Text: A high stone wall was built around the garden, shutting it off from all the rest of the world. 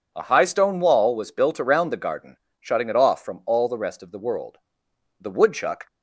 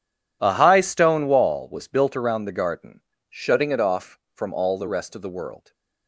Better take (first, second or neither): second